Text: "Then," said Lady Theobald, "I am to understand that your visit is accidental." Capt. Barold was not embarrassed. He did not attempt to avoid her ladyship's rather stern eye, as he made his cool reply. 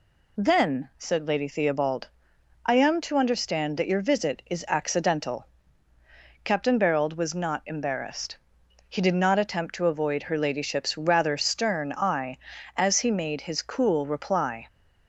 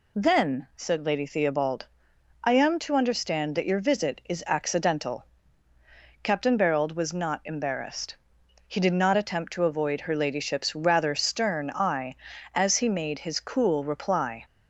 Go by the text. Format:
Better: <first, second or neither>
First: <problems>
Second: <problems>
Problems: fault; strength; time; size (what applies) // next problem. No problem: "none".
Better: neither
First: none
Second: none